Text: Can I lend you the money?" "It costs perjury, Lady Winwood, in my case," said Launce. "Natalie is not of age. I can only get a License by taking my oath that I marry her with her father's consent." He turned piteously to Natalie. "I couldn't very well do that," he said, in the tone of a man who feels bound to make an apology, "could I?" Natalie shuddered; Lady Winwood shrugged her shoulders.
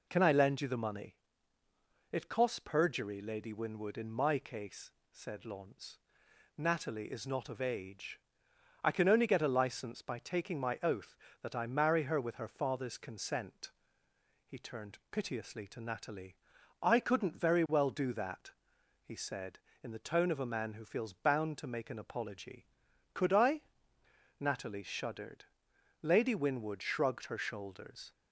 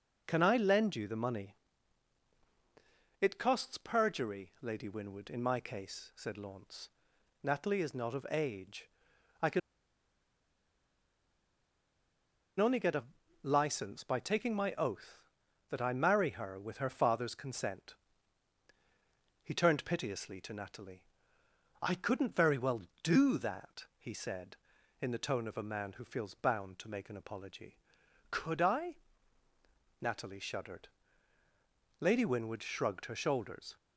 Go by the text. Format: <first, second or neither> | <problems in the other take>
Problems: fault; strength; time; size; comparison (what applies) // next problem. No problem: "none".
first | pauses between "can" and "only"; strong; at 9.5 s; 2.9 s long // pauses between "a" and "License"; at 13.0 s; 0.38 s long